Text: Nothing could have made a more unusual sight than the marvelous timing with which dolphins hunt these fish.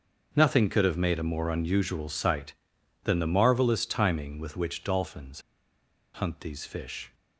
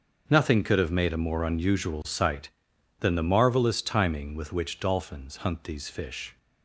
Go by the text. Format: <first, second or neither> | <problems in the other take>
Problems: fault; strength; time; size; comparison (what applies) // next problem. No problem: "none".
second | starts louder than the rest; until 1.3 s; 6.5 dB; also in the second // pauses between "dolphins" and "hunt"; noticeable; at 5.4 s; 0.72 s long